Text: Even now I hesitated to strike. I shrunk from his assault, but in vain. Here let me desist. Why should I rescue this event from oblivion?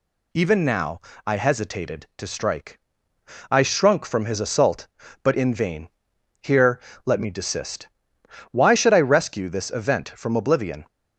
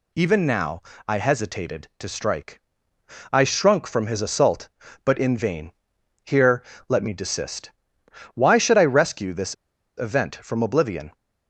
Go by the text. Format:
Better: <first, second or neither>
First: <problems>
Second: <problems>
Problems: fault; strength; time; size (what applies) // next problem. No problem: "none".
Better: first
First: pauses between "now" and "I"; slight; at 0.9 s; 0.26 s long // pauses between "Here" and "let"; slight; at 6.7 s; 0.26 s long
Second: pauses between "now" and "I"; slight; at 0.8 s; 0.26 s long // pauses between "Here" and "let"; slight; at 6.6 s; 0.26 s long // pauses between "this" and "event"; at 9.5 s; 0.44 s long